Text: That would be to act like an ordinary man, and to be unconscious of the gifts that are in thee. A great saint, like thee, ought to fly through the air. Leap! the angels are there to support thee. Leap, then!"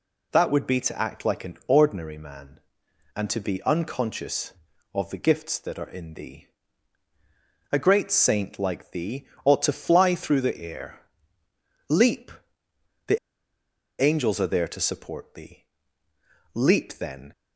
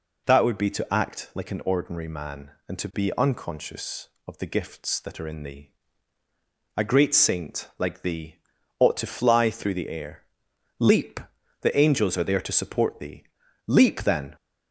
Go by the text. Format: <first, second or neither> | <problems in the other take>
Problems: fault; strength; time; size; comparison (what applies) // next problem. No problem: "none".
second | pauses between "the" and "angels"; noticeable; at 13.1 s; 0.85 s long